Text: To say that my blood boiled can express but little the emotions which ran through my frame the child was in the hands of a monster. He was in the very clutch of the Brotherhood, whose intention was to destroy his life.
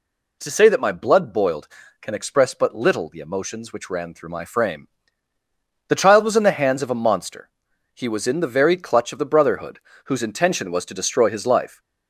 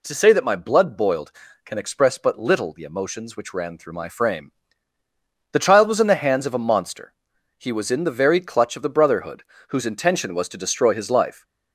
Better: neither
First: pauses between "frame" and "the"; at 4.8 s; 1.0 s long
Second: pauses between "frame" and "the"; at 4.5 s; 1.0 s long

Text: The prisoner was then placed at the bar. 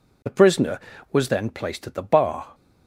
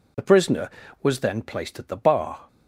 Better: neither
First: none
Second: none

